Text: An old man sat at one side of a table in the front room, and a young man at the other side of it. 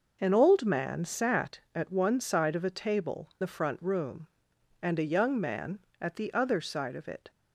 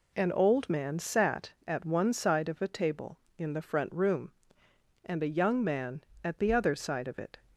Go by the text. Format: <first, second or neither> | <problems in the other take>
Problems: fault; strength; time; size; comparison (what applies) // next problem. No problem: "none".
second | skips "in"; at 3.3 s